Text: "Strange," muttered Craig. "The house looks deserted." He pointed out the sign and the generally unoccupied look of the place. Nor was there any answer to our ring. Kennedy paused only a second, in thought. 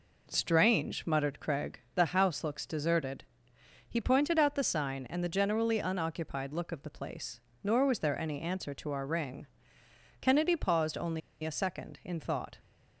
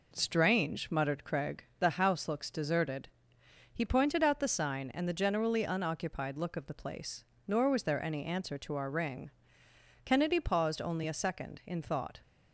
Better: second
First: pauses between "only" and "a"; slight; at 11.2 s; 0.23 s long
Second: none

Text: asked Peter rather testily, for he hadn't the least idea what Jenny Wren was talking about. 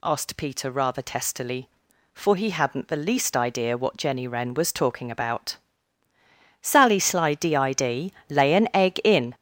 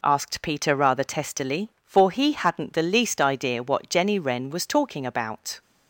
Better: second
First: goes on to say "Sally Sly DID lay an egg in"; strong; from 6.6 s on; 2.7 s long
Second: none

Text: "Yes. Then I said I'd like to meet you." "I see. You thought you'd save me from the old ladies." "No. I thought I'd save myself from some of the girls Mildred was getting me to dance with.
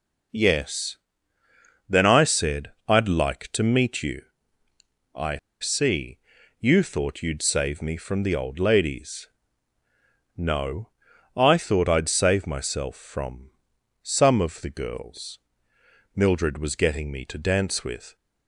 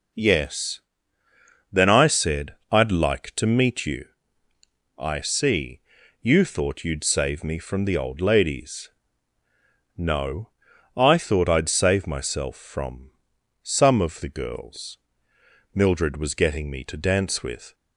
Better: second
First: pauses between "I" and "see"; slight; at 5.3 s; 0.23 s long // pauses between "from" and "some"; noticeable; at 13.5 s; 0.50 s long // pauses between "girls" and "Mildred"; noticeable; at 15.3 s; 0.78 s long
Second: pauses between "from" and "some"; noticeable; at 13.1 s; 0.50 s long // pauses between "girls" and "Mildred"; noticeable; at 14.9 s; 0.78 s long

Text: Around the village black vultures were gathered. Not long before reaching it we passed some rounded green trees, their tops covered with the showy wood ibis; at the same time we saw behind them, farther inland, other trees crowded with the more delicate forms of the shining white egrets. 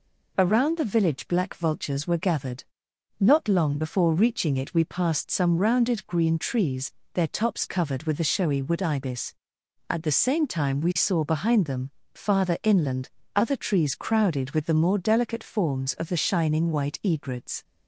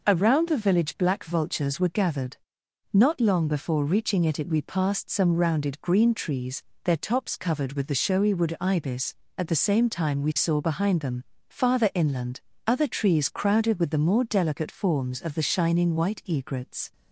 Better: first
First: none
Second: says "it" twice; at 4.3 s

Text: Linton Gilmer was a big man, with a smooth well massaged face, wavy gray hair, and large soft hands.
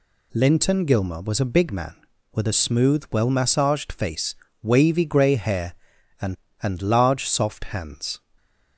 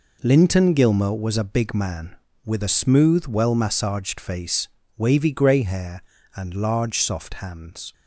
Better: second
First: says "and" twice; at 6.6 s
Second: none

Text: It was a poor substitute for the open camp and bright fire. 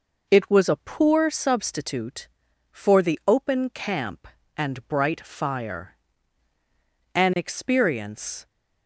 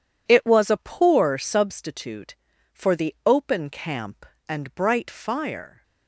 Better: second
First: goes on to say "An experience"; noticeable; from 7.1 s on; 1.3 s long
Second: none

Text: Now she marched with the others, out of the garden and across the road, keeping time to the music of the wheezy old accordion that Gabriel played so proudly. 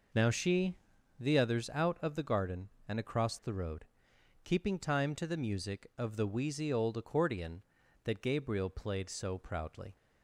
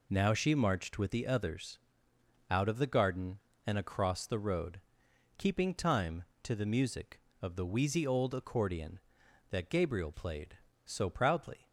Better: second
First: skips "marched with"; at 0.9 s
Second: none

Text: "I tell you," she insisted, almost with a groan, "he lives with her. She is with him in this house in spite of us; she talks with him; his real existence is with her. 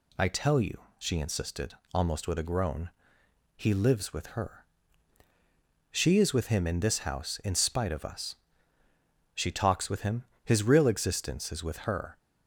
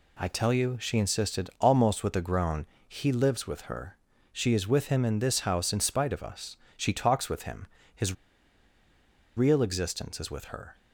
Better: first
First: none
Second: pauses between "his" and "real"; at 8.1 s; 1.2 s long

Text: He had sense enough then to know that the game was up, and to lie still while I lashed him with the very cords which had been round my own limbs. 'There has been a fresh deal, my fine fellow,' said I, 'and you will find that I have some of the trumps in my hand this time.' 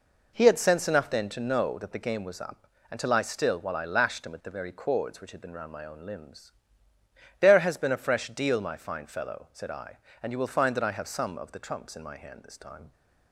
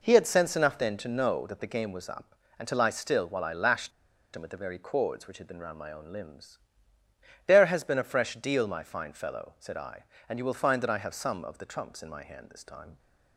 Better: first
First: none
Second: pauses between "lashed" and "him"; at 3.9 s; 0.44 s long

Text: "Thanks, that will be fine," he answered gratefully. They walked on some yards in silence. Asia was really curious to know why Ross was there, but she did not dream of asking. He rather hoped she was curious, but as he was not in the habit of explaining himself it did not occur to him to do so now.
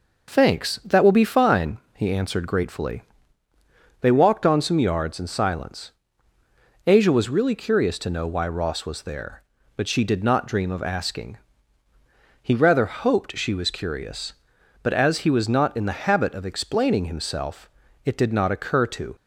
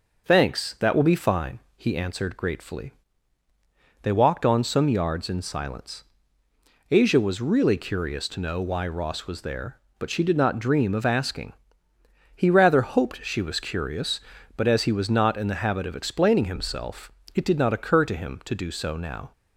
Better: second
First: pauses between "himself" and "it"; at 17.6 s; 0.38 s long // stops before "him to do so now"; at 19.1 s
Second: pauses between "himself" and "it"; slight; at 17.1 s; 0.22 s long

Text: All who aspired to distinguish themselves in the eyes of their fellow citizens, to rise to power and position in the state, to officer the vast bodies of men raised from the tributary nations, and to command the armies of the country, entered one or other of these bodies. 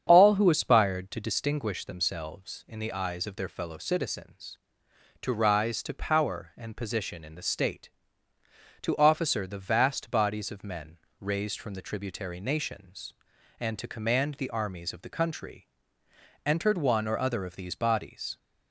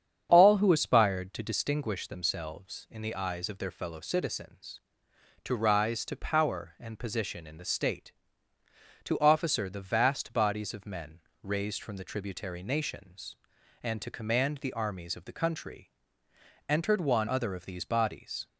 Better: first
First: starts louder than the rest; strong; until 1.0 s; 8.5 dB // pauses between "men" and "raised"; slight; at 10.9 s; 0.24 s long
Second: starts louder than the rest; strong; until 1.3 s; 8.5 dB // pauses between "men" and "raised"; slight; at 11.1 s; 0.24 s long // skips "or"; at 17.2 s

